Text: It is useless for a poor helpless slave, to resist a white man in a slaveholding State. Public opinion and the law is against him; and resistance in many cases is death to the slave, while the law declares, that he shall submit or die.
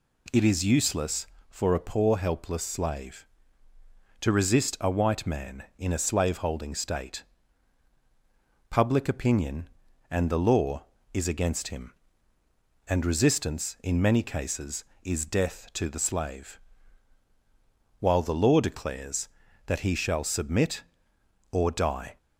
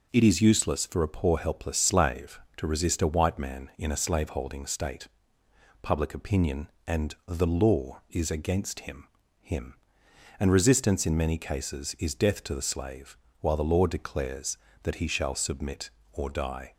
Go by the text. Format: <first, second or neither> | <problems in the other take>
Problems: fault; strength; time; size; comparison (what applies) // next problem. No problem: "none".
first | says "him" twice; at 9.3 s